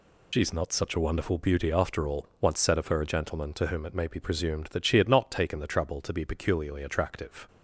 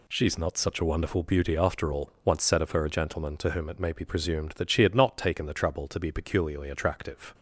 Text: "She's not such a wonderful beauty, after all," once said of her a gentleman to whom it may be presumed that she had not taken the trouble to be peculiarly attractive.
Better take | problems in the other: second | loses the start of "She's"; at 0.3 s; 90 ms

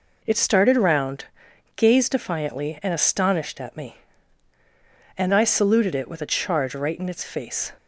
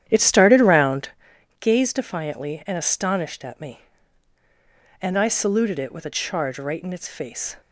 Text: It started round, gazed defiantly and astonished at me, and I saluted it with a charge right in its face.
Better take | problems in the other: first | starts louder than the rest; strong; until 1.2 s; 10.5 dB

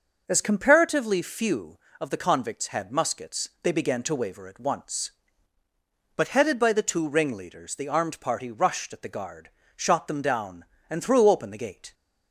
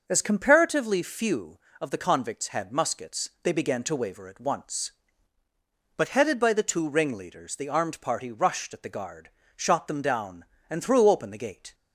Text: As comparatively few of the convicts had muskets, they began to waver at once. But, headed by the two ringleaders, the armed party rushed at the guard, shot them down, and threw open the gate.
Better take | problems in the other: neither | none

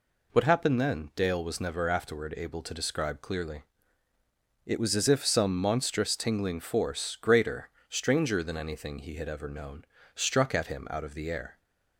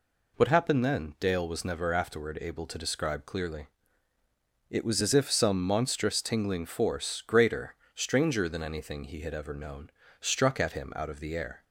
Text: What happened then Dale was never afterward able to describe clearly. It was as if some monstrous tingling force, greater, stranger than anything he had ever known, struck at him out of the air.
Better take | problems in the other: neither | none

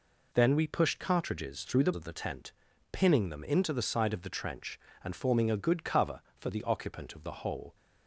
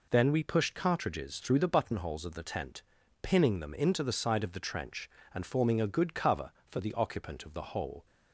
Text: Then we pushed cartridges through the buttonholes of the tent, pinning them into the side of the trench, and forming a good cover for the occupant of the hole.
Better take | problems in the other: second | skips "buttonholes"; at 1.9 s

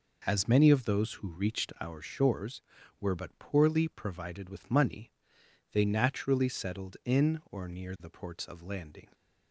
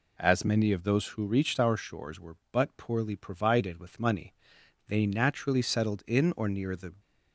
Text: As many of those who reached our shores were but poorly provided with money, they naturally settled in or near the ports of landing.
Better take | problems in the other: first | stops before "ports of landing"; at 6.9 s

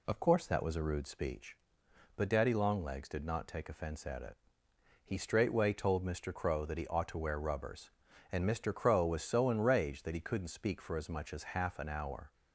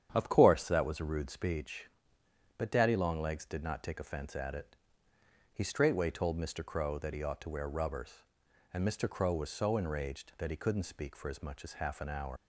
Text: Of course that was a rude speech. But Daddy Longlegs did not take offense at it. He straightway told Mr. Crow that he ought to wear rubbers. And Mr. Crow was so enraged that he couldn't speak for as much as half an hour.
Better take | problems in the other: first | starts louder than the rest; strong; until 1.1 s; 9 dB // leaves "hour" unfinished; at 12.3 s; 100 ms

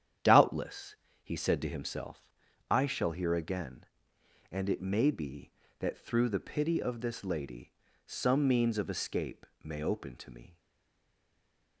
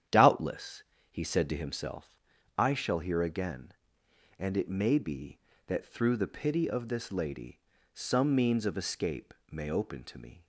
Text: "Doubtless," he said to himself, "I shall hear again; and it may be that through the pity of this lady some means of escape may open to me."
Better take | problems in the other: second | starts louder than the rest; strong; until 1.5 s; 9.5 dB; strong in the second // pauses between "lady" and "some"; slight; at 7.7 s; 0.34 s long; slight in the second // pauses between "escape" and "may"; slight; at 9.4 s; 0.18 s long; slight in the second // stays silent after the last word; noticeable; from 10.5 s on; 1.3 s long

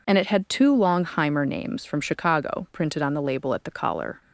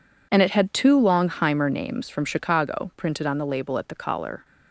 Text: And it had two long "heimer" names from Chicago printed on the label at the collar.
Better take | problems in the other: first | gets quieter; strong; throughout; 13 dB

